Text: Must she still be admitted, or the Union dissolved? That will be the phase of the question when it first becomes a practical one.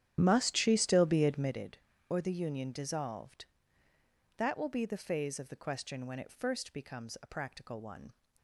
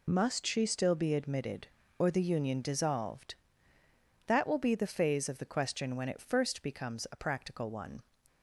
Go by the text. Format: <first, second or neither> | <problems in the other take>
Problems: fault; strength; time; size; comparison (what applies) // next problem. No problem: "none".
second | starts louder than the rest; strong; until 1.7 s; 10.5 dB